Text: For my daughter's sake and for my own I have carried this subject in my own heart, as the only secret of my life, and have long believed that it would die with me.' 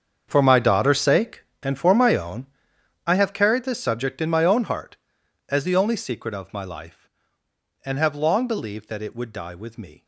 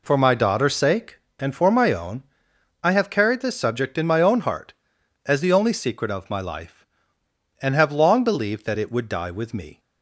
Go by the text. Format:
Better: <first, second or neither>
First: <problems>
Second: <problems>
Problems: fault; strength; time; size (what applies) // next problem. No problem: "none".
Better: second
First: gets quieter; strong; throughout; 16 dB // pauses between "own" and "I"; noticeable; at 2.4 s; 0.58 s long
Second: pauses between "own" and "I"; noticeable; at 2.2 s; 0.58 s long